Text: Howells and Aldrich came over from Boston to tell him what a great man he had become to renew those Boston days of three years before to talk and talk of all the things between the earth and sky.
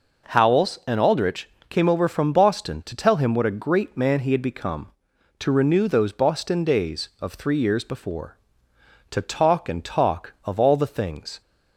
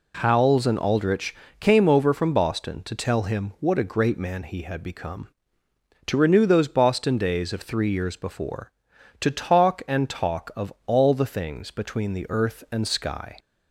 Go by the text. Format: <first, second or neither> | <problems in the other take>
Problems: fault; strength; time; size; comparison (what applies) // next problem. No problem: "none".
second | pauses between "Aldrich" and "came"; slight; at 1.5 s; 0.18 s long; slight in the second // stops before "between the earth and sky"; at 11.4 s